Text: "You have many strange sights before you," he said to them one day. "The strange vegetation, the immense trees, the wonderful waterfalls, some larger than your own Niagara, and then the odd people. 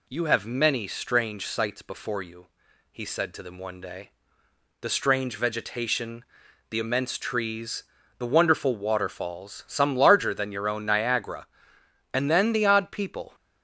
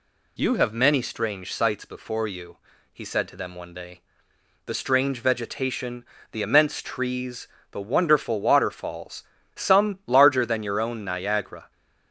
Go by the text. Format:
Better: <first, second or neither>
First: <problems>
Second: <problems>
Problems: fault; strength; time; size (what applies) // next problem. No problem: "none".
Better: first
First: none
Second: stops before "and then the odd people"; at 11.7 s